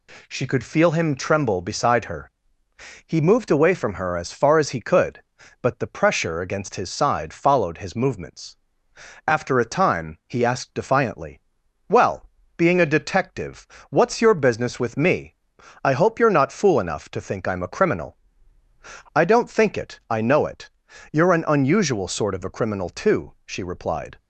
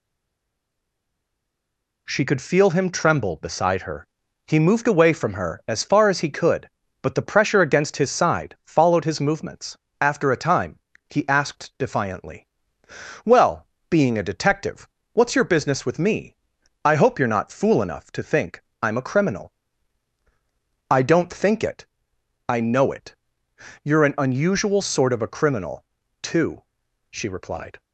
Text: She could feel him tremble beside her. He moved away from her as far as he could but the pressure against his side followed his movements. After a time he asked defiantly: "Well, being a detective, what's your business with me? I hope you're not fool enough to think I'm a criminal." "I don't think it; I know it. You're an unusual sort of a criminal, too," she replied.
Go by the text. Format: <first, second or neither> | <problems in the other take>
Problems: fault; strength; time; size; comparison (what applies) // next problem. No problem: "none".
first | stays silent before the first word; noticeable; until 2.0 s; 2.0 s long // pauses between "time" and "he"; slight; at 10.7 s; 0.32 s long // pauses between "think" and "I'm"; slight; at 18.6 s; 0.22 s long